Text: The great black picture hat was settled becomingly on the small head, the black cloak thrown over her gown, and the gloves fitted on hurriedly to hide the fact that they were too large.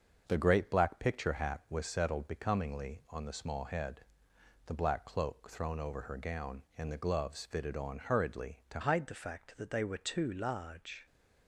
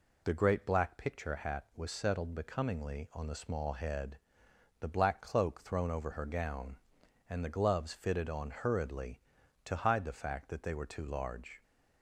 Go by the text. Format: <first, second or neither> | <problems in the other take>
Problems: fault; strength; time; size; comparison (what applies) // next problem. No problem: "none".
second | starts louder than the rest; until 1.2 s; 6.5 dB // changes voice at "hide"; from 8.8 s on; 2.2 s long